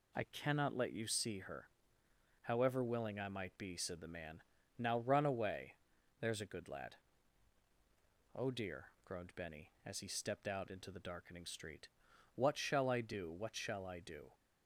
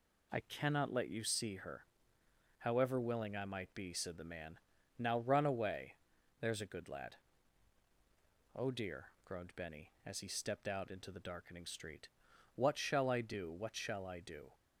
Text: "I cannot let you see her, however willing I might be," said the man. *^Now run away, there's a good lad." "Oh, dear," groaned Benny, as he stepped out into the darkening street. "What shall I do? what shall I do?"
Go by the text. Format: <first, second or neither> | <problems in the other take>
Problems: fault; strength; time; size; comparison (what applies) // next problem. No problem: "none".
neither | none